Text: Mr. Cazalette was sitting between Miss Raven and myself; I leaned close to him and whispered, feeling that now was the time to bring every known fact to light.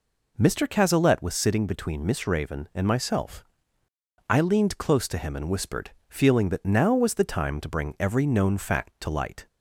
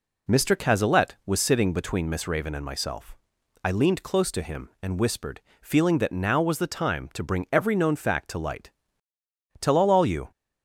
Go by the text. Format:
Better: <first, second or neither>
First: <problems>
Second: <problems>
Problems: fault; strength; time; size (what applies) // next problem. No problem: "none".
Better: first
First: none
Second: goes on to say "Tell all all you"; noticeable; from 9.6 s on; 0.70 s long